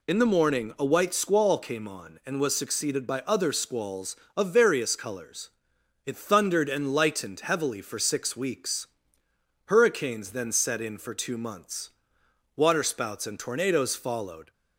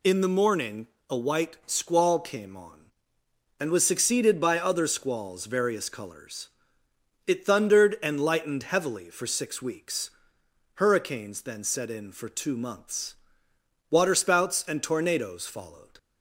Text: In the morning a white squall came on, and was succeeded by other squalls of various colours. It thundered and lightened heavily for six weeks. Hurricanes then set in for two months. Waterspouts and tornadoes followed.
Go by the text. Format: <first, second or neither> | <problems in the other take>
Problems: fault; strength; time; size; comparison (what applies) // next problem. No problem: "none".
first | pauses between "morning" and "a"; slight; at 0.8 s; 0.22 s long // skips "of"; at 5.4 s